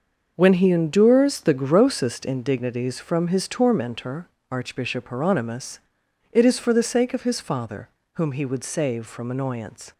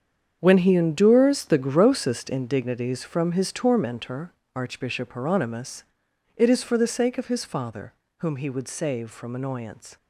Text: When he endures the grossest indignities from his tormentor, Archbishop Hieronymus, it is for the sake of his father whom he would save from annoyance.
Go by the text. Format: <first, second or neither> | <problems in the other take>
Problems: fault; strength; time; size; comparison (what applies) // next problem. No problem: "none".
first | gets quieter; strong; throughout; 11.5 dB // starts louder than the rest; strong; until 1.4 s; 8 dB; also in the first // pauses between "father" and "whom"; slight; at 7.9 s; 0.28 s long; slight in the first